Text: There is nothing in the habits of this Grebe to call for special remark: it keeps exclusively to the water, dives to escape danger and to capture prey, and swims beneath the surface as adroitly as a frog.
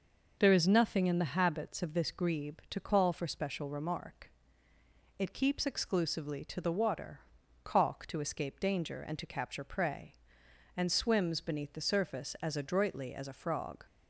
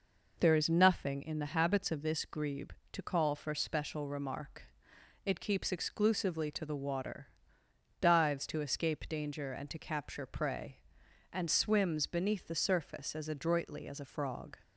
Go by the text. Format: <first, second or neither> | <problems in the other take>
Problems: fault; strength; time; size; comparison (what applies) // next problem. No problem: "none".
second | says "caulk" for "dives"; at 7.6 s